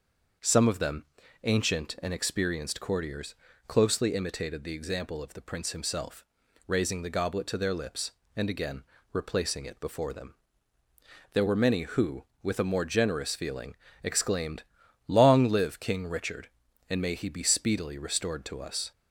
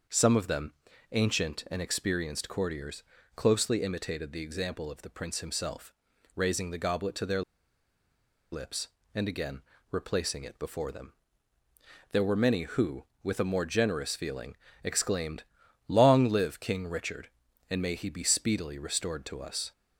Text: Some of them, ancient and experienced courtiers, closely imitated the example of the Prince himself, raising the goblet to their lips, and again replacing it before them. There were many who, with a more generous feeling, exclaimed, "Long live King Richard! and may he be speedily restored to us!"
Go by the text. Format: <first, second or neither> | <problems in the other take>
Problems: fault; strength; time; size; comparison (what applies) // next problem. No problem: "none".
first | starts louder than the rest; until 1.4 s; 6 dB; also in the first // pauses between "their" and "lips"; at 7.4 s; 1.1 s long // pauses between "again" and "replacing"; slight; at 9.6 s; 0.30 s long; slight in the first